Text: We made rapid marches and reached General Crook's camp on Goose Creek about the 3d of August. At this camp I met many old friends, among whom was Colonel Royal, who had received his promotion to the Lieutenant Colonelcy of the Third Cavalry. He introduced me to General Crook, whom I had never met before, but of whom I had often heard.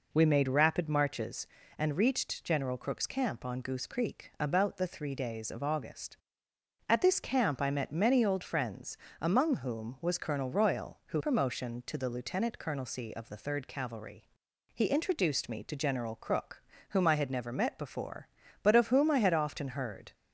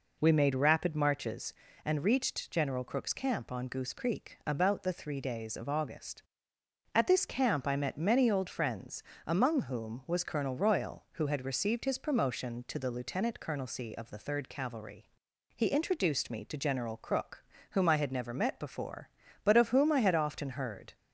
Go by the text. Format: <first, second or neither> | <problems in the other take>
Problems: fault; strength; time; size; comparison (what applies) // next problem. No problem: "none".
second | skips "had received his"; at 11.2 s